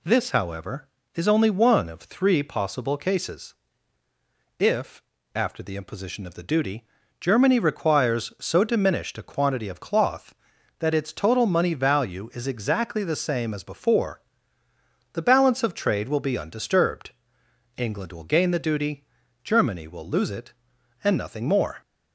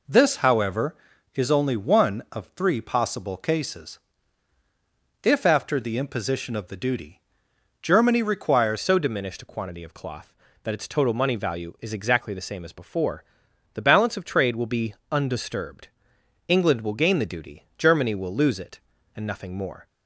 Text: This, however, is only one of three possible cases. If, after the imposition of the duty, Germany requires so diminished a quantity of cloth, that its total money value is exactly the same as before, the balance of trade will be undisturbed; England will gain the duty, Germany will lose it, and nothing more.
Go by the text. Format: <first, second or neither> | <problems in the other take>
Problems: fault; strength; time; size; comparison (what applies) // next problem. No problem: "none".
first | changes voice at "so"; from 8.8 s on; 11.0 s long // pauses between "be" and "undisturbed"; slight; at 14.9 s; 0.18 s long